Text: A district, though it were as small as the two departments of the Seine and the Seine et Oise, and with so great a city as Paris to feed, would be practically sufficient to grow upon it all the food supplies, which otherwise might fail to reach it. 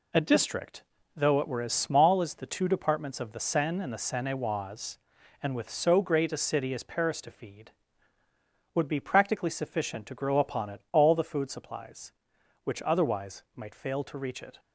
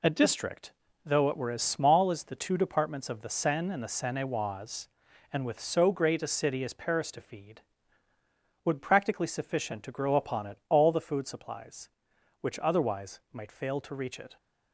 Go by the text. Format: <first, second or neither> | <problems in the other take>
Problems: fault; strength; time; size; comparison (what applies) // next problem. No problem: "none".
first | skips "be"; at 8.7 s